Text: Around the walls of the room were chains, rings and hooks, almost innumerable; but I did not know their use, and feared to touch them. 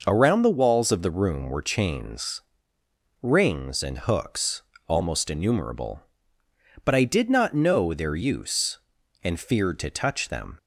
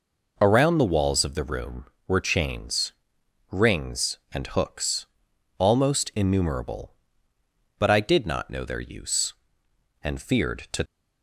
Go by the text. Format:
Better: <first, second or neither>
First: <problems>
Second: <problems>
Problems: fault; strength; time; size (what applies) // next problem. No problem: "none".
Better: first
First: none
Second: stops before "touch them"; at 10.8 s